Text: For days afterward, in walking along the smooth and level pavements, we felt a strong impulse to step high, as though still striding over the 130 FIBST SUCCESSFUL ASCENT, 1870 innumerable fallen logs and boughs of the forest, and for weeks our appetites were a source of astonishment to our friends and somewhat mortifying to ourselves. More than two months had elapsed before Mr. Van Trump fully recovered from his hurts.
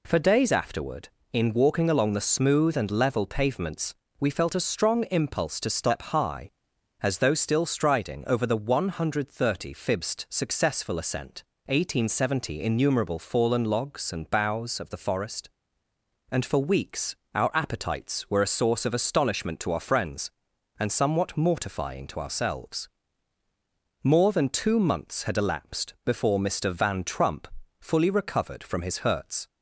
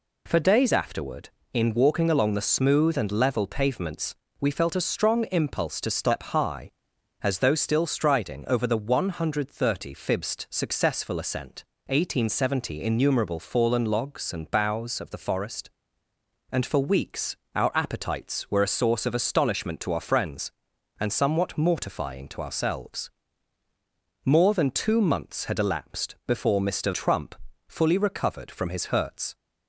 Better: first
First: pauses between "weeks" and "our"; slight; at 17.1 s; 0.18 s long // pauses between "Trump" and "fully"; slight; at 27.4 s; 0.34 s long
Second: pauses between "weeks" and "our"; slight; at 17.3 s; 0.18 s long // skips "Van"; at 26.9 s // pauses between "Trump" and "fully"; slight; at 27.3 s; 0.34 s long

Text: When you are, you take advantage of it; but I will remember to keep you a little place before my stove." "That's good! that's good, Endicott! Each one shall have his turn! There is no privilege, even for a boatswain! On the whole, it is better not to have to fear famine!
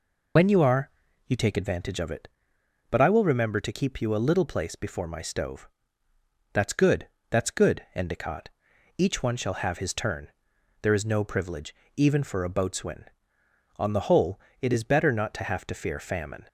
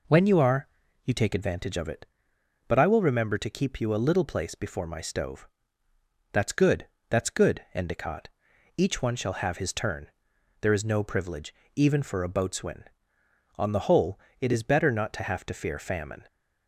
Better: second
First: loses the start of "When"; at 0.3 s; 60 ms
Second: none

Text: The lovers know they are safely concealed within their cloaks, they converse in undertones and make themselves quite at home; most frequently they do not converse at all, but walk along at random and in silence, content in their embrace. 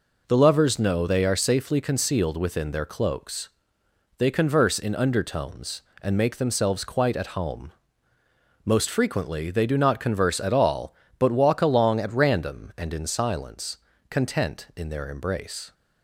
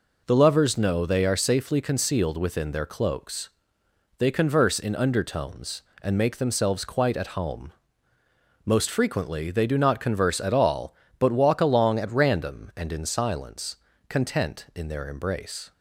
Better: neither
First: none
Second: none

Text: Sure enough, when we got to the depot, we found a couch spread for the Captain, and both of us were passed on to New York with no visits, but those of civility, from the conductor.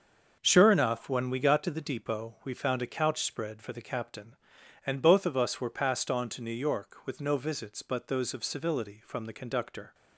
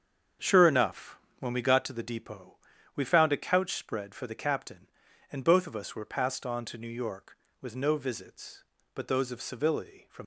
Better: first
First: starts louder than the rest; until 1.4 s; 6.5 dB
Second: starts louder than the rest; strong; until 1.6 s; 7 dB // stops before "the conductor"; at 10.2 s

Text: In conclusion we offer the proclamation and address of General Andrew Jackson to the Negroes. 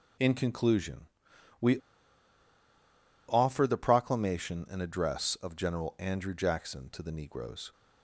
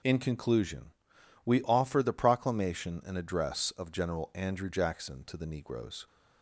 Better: second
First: pauses between "conclusion" and "we"; noticeable; at 1.0 s; 0.54 s long // pauses between "we" and "offer"; strong; at 1.7 s; 1.5 s long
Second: pauses between "conclusion" and "we"; noticeable; at 0.9 s; 0.54 s long

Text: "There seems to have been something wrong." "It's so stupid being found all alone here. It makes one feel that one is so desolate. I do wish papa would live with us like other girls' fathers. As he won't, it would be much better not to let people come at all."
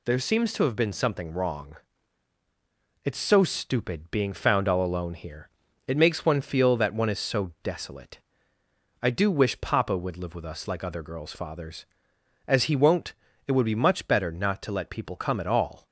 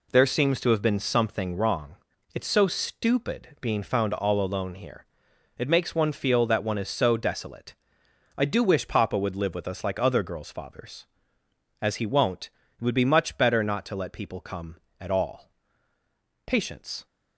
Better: first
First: none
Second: goes on to say "Patience"; from 16.4 s on; 0.58 s long

